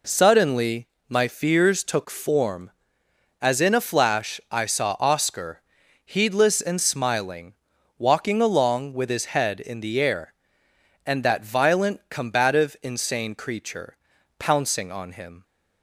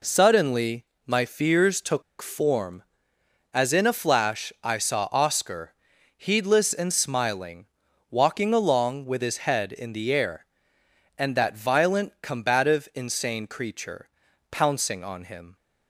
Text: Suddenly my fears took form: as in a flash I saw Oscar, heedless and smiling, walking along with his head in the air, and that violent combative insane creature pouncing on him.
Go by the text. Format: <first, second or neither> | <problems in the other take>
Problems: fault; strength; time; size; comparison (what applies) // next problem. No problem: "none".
first | pauses between "Suddenly" and "my"; slight; at 0.8 s; 0.24 s long; slight in the first // pauses between "took" and "form"; slight; at 2.0 s; 0.18 s long // pauses between "creature" and "pouncing"; at 14.0 s; 0.42 s long; also in the first